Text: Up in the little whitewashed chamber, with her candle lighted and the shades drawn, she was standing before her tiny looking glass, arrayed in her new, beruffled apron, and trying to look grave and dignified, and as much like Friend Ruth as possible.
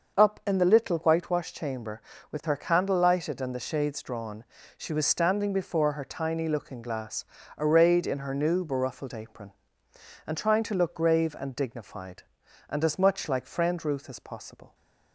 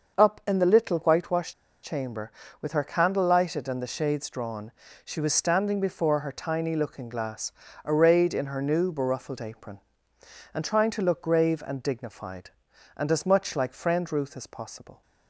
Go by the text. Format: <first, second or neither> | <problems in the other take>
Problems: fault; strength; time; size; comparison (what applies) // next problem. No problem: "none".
first | starts louder than the rest; until 1.2 s; 6 dB; also in the first // pauses between "whitewashed" and "chamber"; slight; at 1.5 s; 0.32 s long